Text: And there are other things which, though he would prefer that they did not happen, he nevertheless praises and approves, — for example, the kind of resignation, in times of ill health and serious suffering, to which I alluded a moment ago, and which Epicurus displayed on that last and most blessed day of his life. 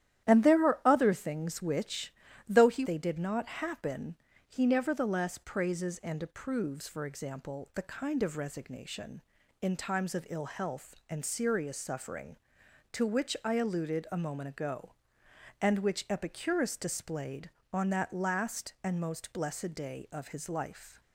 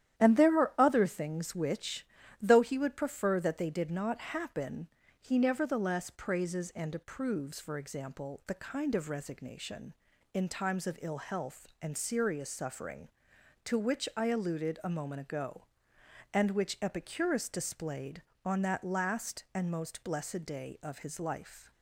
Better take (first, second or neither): second